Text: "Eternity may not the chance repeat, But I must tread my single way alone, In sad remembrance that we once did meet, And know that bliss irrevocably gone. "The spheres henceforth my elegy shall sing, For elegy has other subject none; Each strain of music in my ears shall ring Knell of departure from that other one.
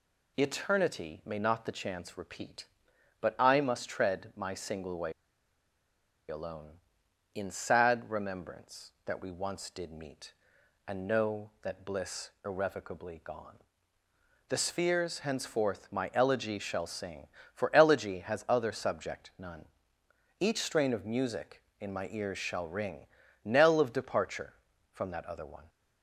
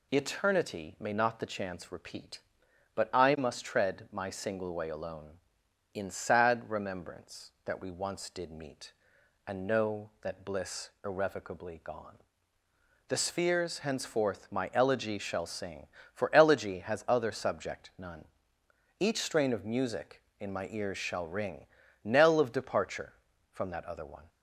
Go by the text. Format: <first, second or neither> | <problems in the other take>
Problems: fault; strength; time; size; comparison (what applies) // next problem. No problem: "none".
second | pauses between "way" and "alone"; at 5.1 s; 1.1 s long // pauses between "ring" and "Knell"; slight; at 23.0 s; 0.36 s long; slight in the second